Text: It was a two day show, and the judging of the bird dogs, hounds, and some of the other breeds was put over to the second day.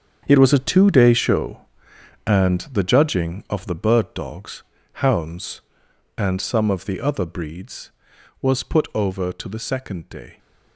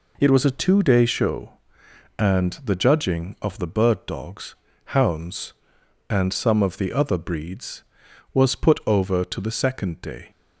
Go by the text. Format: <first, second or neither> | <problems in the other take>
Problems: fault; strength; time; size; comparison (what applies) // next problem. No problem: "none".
second | gets quieter; strong; throughout; 12.5 dB